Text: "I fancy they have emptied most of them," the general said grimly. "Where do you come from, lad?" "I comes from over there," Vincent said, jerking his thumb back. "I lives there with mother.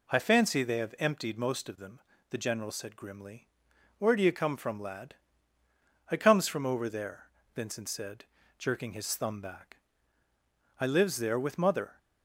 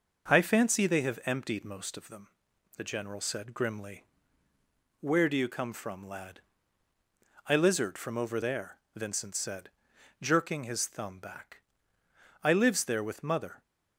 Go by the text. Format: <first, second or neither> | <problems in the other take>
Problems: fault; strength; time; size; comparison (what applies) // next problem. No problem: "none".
first | starts louder than the rest; noticeable; until 1.3 s; 6 dB // says "lizard" for "comes"; at 7.5 s